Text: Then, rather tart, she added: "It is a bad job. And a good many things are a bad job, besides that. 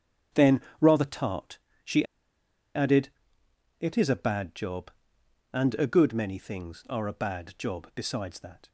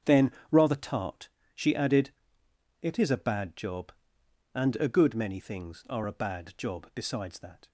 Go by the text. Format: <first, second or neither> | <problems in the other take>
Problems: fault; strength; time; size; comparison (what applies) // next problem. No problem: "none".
second | starts louder than the rest; strong; until 1.5 s; 7.5 dB; strong in the second // pauses between "she" and "added"; noticeable; at 2.0 s; 0.69 s long